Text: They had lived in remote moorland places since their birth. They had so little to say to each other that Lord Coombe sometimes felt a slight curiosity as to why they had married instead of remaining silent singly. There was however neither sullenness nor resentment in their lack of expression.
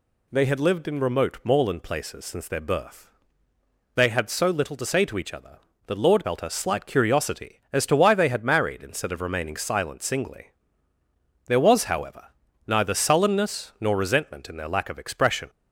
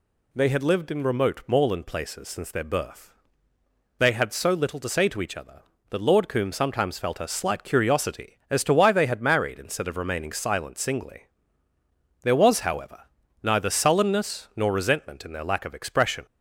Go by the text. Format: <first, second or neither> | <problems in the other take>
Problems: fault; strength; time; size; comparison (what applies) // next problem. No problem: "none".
second | skips "Coombe sometimes"; at 6.2 s // pauses between "however" and "neither"; at 12.2 s; 0.42 s long; also in the second